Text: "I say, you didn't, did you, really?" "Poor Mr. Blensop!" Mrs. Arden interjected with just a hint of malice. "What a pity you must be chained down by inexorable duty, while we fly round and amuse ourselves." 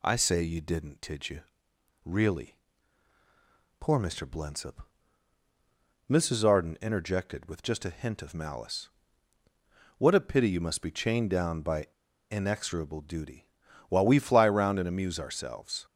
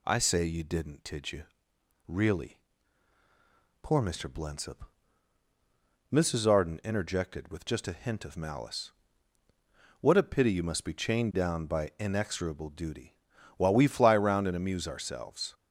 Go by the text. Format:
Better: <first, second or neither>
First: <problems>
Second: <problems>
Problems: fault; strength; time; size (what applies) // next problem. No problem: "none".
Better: second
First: pauses between "by" and "inexorable"; at 11.8 s; 0.44 s long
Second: none